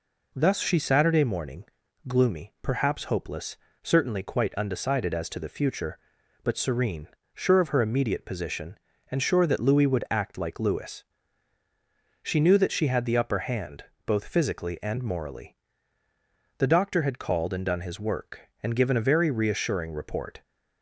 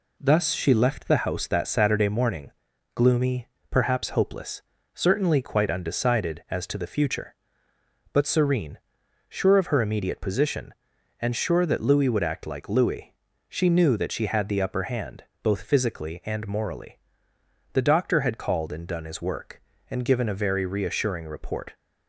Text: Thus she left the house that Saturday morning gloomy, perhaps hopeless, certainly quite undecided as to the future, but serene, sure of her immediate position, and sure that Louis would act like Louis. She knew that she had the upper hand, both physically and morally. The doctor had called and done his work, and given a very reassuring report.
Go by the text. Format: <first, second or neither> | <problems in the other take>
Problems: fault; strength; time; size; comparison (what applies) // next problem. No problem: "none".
second | skips "left the house that"; at 0.7 s // pauses between "morning" and "gloomy"; at 1.6 s; 0.44 s long; also in the second